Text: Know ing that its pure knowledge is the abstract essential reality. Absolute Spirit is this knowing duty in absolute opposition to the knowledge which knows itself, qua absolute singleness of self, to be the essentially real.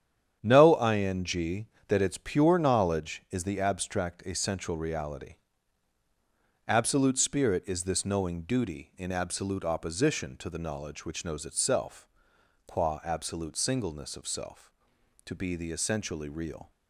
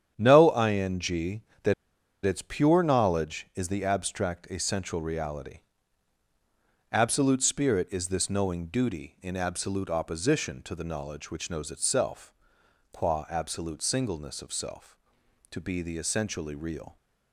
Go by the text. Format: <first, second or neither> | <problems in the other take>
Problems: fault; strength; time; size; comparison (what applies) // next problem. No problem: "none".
first | starts louder than the rest; strong; until 1.1 s; 9 dB; strong in the first // pauses between "that" and "its"; noticeable; at 1.7 s; 0.51 s long